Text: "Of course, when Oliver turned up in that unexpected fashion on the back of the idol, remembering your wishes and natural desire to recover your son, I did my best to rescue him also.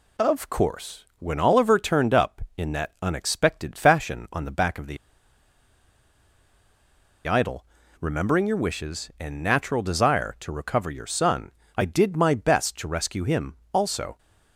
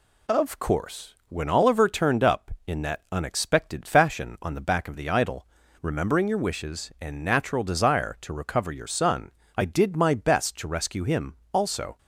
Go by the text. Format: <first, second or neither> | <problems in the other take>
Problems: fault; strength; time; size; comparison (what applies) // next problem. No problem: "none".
second | pauses between "the" and "idol"; strong; at 4.9 s; 2.3 s long